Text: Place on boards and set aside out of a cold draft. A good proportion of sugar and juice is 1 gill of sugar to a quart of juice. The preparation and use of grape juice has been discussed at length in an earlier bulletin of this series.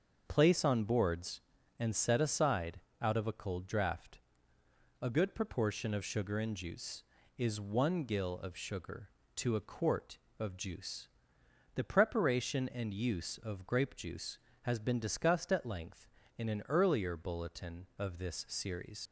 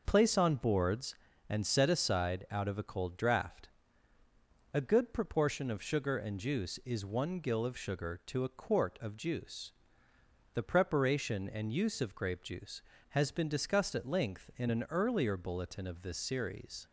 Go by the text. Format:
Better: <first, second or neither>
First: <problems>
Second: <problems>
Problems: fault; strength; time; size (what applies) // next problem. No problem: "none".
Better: second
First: starts louder than the rest; until 1.2 s; 6.5 dB // pauses between "aside" and "out"; slight; at 2.7 s; 0.20 s long // leaves "series" unfinished; at 19.0 s; 75 ms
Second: none